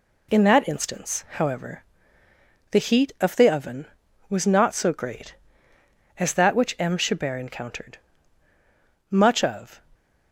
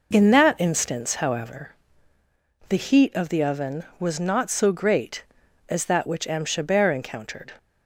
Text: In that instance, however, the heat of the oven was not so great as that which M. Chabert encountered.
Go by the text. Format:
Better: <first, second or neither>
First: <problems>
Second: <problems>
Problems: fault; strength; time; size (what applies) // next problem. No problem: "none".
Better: second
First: goes on to say "Much of"; noticeable; from 9.1 s on; 0.70 s long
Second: none